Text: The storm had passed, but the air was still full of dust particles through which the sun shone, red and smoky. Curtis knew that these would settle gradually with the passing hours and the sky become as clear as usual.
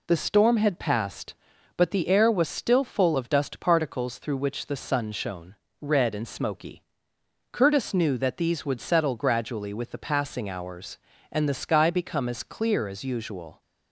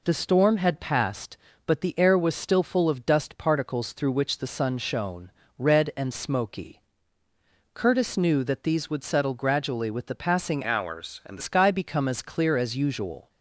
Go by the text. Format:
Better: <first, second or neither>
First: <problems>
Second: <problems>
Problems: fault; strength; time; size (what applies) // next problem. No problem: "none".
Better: first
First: none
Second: changes voice from "hours" to "the"; from 10.6 to 11.4 s; 0.8 s long